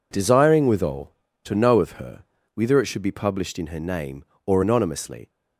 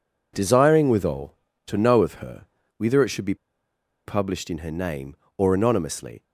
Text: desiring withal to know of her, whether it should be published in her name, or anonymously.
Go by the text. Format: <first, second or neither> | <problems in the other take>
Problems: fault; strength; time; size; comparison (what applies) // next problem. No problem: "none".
first | pauses between "be" and "published"; noticeable; at 3.3 s; 0.71 s long